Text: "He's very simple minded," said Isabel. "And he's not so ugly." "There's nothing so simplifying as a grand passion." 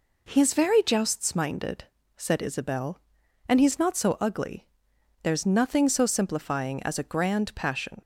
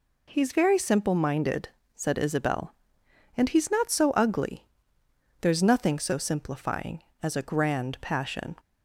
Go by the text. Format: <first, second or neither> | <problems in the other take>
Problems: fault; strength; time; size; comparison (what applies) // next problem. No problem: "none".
second | says "jousts" for "simple"; at 0.8 s